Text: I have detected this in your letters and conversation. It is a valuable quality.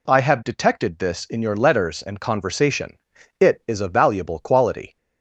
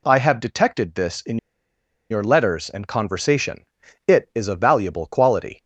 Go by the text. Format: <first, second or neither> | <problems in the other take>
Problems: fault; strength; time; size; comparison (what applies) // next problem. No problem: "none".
first | pauses between "in" and "your"; noticeable; at 1.3 s; 0.72 s long